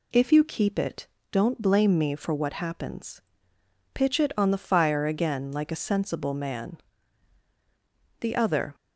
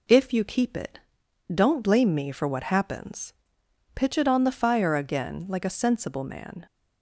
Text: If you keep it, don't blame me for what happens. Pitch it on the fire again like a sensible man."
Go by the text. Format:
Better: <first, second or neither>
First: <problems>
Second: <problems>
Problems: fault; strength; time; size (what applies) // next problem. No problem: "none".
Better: second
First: goes on to say "The other"; from 8.1 s on; 0.56 s long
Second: none